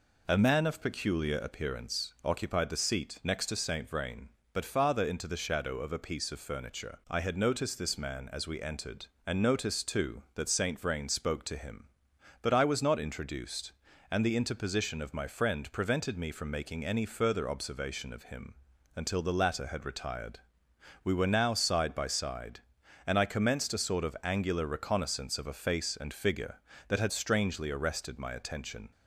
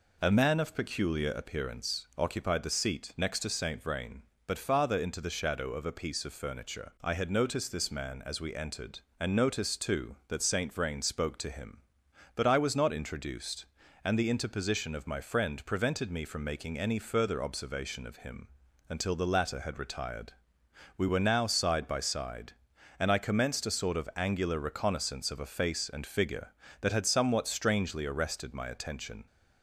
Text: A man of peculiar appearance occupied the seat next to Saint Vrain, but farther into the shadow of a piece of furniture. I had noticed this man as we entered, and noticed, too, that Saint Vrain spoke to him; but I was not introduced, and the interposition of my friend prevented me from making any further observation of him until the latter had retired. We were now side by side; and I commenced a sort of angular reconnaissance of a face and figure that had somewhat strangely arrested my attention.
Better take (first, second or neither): second